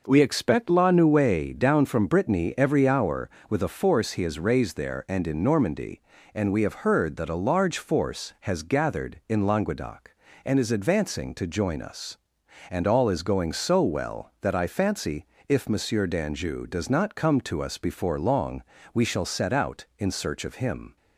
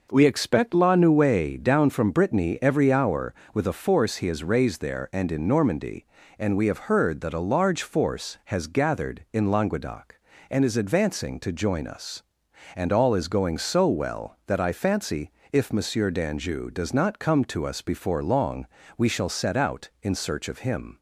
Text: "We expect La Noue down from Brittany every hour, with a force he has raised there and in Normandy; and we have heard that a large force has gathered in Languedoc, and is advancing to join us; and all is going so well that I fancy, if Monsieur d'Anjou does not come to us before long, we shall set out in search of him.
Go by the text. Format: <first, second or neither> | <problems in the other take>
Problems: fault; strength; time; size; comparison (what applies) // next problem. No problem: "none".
neither | none